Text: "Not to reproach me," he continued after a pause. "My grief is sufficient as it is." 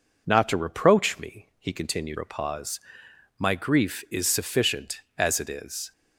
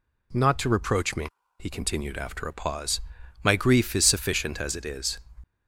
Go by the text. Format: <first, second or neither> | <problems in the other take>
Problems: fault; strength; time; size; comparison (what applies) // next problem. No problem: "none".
second | skips "after"; at 2.1 s